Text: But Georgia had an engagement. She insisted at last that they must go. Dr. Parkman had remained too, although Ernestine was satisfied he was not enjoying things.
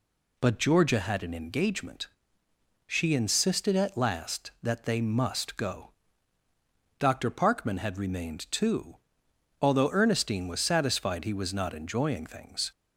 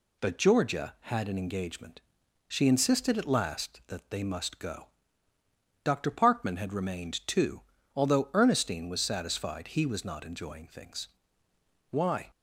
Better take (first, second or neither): first